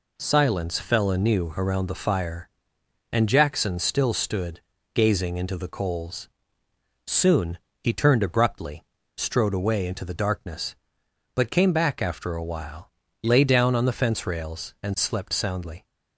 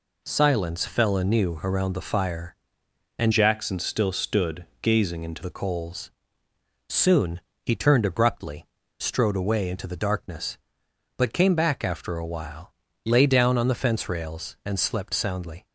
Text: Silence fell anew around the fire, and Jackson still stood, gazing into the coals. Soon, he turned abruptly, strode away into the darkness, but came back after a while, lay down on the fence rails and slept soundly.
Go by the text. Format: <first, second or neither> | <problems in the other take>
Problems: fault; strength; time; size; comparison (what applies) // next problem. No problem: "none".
first | changes voice from "Jackson" to "into"; from 3.3 to 5.4 s; 2.1 s long